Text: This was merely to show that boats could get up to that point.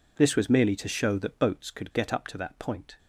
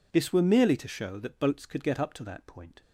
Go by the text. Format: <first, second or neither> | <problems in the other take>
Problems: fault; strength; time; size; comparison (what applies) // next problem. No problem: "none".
first | says "were" for "was"; at 0.3 s